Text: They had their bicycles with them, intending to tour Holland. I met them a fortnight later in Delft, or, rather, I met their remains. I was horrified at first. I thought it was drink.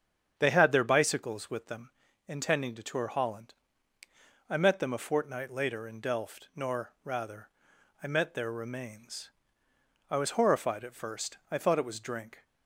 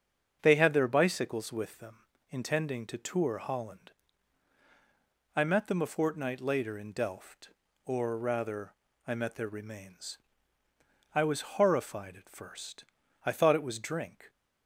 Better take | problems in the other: second | starts louder than the rest; strong; until 1.3 s; 8 dB; also in the second // says "nor" for "or"; at 6.5 s

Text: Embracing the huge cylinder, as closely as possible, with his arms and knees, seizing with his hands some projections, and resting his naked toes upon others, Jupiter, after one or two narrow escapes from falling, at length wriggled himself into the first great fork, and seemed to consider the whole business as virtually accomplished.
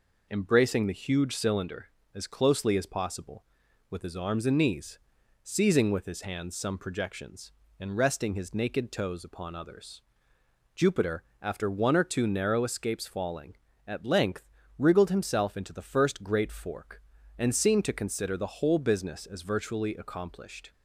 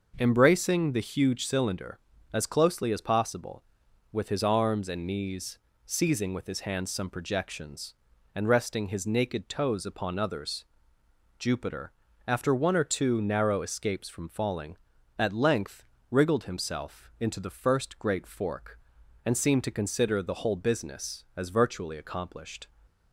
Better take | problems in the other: second | skips "from"; at 13.0 s // pauses between "length" and "wriggled"; slight; at 14.4 s; 0.34 s long; slight in the second

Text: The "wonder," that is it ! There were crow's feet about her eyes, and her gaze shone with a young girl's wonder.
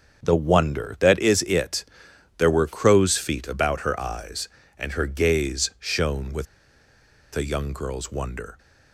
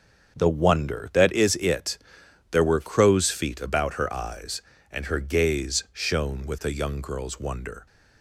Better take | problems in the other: second | starts louder than the rest; until 1.2 s; 7 dB; also in the second // pauses between "with" and "a"; noticeable; at 6.4 s; 0.89 s long

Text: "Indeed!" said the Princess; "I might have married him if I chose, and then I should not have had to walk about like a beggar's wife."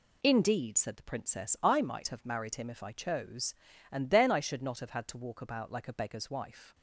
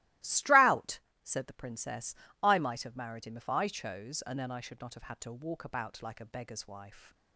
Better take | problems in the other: first | starts louder than the rest; strong; until 1.4 s; 17.5 dB // says "Strout" for "Indeed"; at 0.2 s

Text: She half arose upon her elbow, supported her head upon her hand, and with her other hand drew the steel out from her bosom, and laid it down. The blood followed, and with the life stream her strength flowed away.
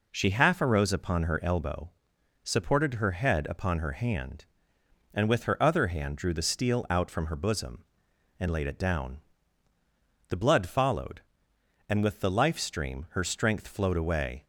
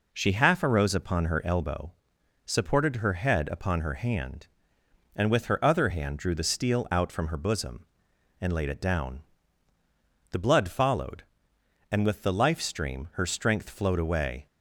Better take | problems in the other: neither | none

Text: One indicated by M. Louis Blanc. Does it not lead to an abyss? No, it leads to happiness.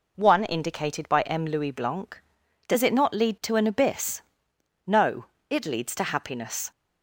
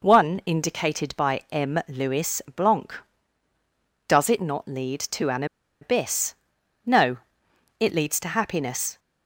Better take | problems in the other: first | pauses between "Louis" and "Blanc"; slight; at 2.4 s; 0.16 s long // pauses between "an" and "abyss"; at 5.4 s; 0.36 s long

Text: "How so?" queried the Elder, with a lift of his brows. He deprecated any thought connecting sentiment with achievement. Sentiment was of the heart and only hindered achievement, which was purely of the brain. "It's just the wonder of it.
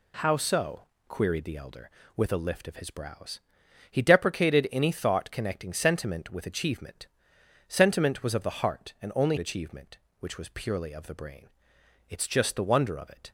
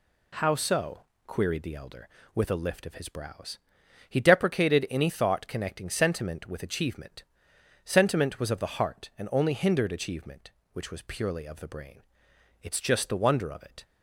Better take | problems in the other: second | skips "hindered"; at 9.3 s

